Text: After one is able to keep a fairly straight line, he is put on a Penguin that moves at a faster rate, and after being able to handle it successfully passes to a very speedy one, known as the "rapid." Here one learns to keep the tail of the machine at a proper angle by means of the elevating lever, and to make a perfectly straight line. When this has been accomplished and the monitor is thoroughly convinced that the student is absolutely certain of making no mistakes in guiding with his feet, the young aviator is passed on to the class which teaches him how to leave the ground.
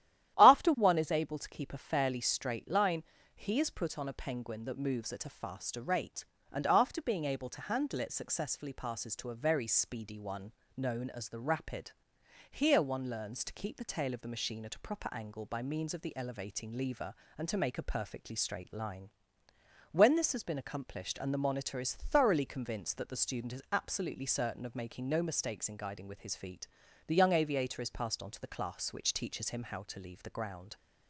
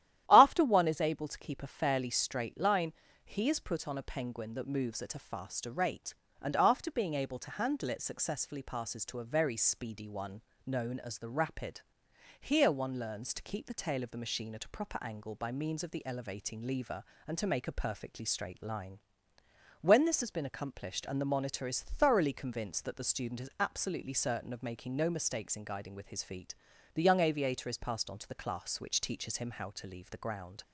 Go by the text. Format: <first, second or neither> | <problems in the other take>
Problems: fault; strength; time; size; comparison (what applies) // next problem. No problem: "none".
neither | starts louder than the rest; strong; the same in both